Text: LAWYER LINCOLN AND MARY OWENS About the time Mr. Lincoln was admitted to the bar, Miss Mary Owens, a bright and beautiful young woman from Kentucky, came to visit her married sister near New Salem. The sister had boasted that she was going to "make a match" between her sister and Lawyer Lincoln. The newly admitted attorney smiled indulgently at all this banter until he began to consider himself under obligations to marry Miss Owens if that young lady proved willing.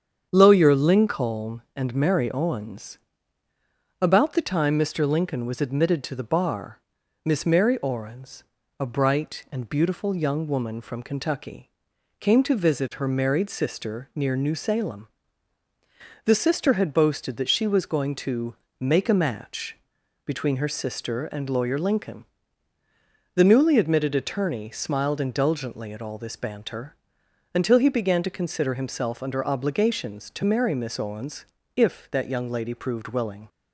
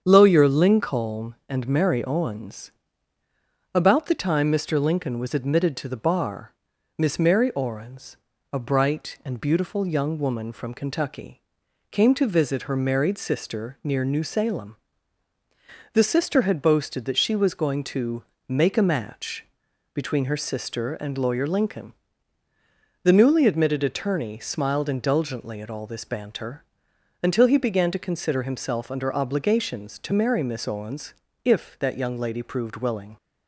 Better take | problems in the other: neither | starts louder than the rest; strong; the same in both // pauses between "OWENS" and "About"; the same in both // pauses between "to" and "make"; slight; the same in both // pauses between "match" and "between"; noticeable; the same in both // pauses between "banter" and "until"; noticeable; the same in both // pauses between "Owens" and "if"; slight; the same in both

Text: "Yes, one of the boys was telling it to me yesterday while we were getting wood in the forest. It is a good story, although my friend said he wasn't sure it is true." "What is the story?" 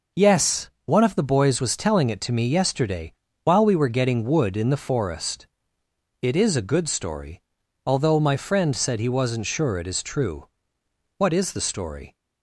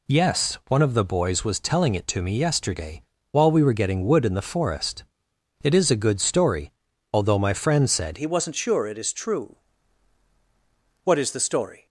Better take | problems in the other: first | pauses between "yesterday" and "while"; slight; at 3.0 s; 0.30 s long; slight in the first // changes voice at "he"; from 8.1 s on; 3.7 s long

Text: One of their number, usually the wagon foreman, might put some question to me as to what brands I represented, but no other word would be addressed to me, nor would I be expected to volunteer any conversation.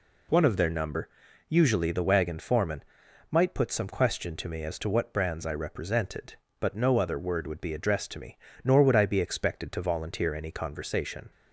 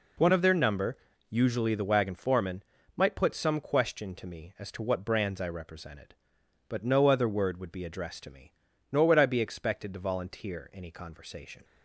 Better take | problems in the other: first | changes voice at "of"; from 0.3 s on; 11.3 s long

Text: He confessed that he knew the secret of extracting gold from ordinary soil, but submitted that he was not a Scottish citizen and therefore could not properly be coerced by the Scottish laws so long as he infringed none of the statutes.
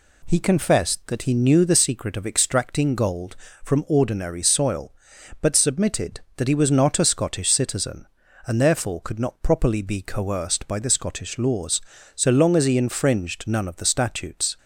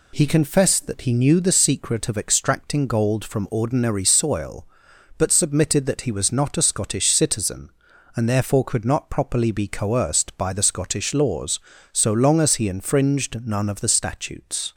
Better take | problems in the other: neither | none

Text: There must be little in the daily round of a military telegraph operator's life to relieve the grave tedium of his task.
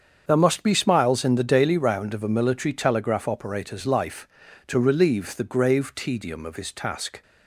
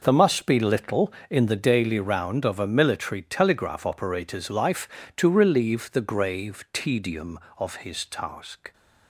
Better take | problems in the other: second | starts louder than the rest; strong; until 1.2 s; 7 dB // says "smiles" for "little"; at 0.7 s

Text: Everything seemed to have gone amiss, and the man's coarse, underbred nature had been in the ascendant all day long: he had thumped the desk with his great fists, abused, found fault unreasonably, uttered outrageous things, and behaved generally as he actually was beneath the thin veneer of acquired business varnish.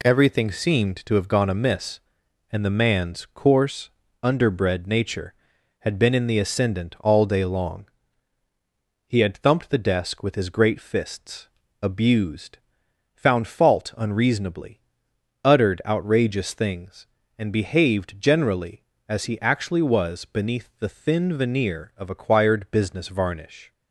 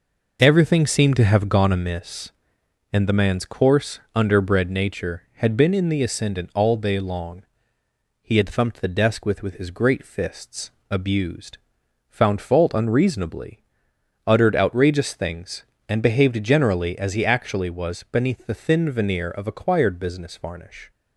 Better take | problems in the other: first | says "with" twice; at 9.4 s

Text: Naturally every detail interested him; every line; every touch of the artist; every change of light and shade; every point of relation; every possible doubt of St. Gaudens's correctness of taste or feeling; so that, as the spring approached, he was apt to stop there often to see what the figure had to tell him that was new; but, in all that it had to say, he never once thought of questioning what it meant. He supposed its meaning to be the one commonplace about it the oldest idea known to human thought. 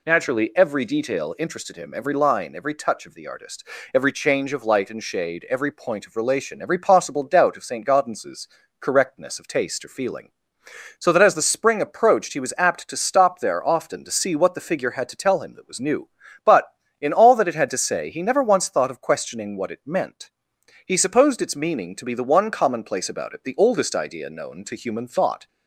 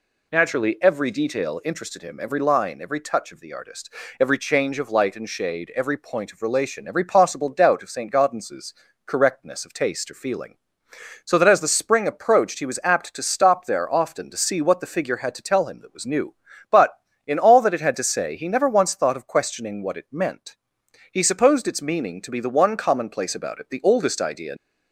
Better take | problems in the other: first | pauses between "Gaudens's" and "correctness"; slight; at 8.7 s; 0.32 s long; slight in the first // stops before "known to human thought"; at 24.5 s

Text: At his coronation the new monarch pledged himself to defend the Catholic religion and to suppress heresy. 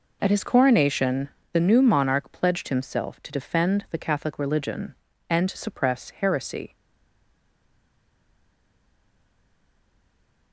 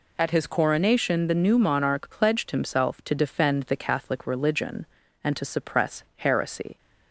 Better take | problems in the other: second | pauses between "coronation" and "the"; slight; at 1.2 s; 0.24 s long // stays silent after the last word; strong; from 6.7 s on; 3.8 s long

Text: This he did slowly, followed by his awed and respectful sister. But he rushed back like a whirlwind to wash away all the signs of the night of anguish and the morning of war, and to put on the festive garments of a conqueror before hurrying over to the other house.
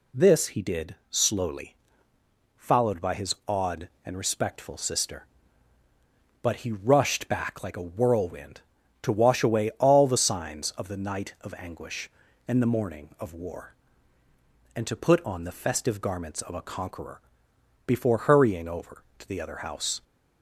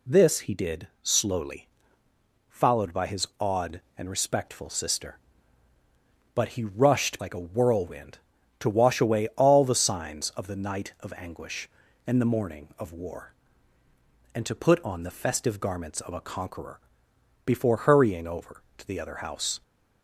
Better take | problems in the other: first | pauses between "did" and "slowly"; slight; at 0.8 s; 0.16 s long; slight in the first // skips "back"; at 7.2 s // pauses between "conqueror" and "before"; noticeable; at 16.7 s; 0.68 s long; noticeable in the first

